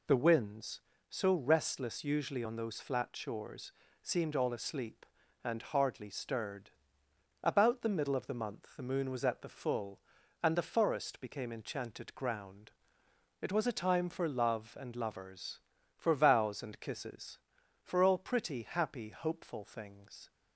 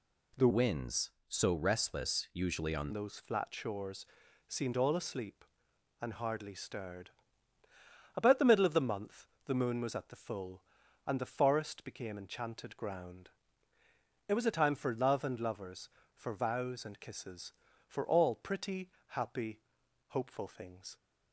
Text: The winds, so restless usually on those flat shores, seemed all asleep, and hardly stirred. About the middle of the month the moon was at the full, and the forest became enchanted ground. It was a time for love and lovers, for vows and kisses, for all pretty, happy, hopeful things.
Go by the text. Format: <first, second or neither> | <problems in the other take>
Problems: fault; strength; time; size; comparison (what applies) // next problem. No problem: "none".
first | changes voice from "winds" to "on"; from 0.5 to 2.9 s; 2.4 s long // pauses between "month" and "the"; slight; at 9.2 s; 0.20 s long